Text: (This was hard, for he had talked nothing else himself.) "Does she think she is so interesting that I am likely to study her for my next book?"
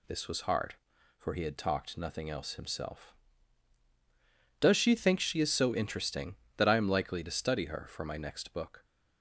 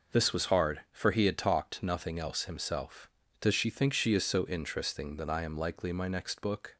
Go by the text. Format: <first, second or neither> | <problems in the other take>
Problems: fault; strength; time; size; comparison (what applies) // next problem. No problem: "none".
first | skips "to study her for"; at 5.9 s